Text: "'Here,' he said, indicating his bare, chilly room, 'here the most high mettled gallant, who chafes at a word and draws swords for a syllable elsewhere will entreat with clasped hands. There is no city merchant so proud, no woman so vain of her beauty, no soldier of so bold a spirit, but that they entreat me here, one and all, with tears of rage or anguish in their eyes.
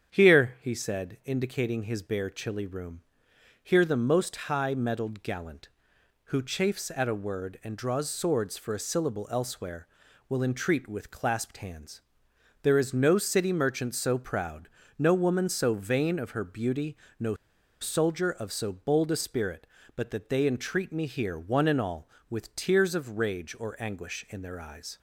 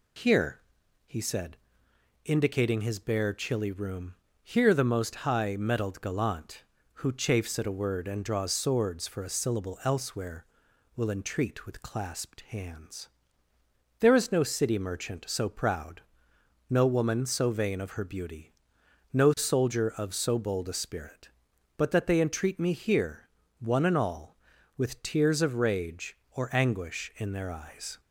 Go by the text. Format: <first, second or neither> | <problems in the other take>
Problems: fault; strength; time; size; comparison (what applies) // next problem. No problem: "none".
second | starts louder than the rest; strong; until 1.1 s; 8 dB // pauses between "no" and "soldier"; at 17.3 s; 0.45 s long